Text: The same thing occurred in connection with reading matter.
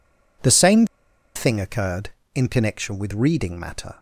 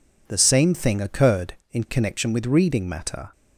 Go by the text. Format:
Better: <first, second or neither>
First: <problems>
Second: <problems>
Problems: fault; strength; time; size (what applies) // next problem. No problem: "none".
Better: second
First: pauses between "same" and "thing"; noticeable; at 0.8 s; 0.49 s long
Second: none